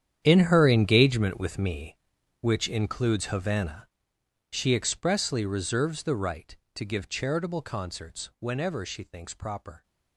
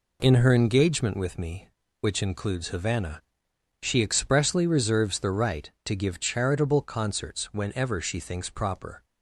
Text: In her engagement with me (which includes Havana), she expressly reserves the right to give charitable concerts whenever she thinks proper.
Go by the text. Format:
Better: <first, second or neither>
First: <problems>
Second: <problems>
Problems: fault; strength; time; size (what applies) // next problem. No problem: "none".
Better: second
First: gets quieter; strong; throughout; 15.5 dB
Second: none